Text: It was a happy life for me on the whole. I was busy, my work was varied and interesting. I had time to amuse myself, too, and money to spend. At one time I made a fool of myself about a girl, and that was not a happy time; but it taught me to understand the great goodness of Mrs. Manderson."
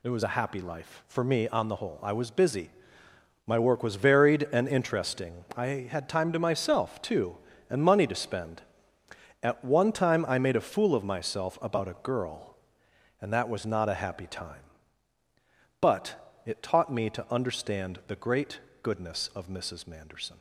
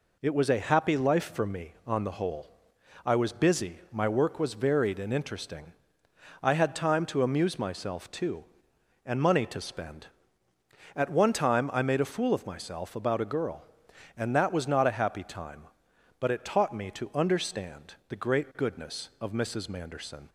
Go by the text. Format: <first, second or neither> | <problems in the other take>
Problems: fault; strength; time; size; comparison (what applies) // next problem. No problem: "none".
second | skips "amuse"; at 6.3 s // pauses between "great" and "goodness"; slight; at 18.5 s; 0.22 s long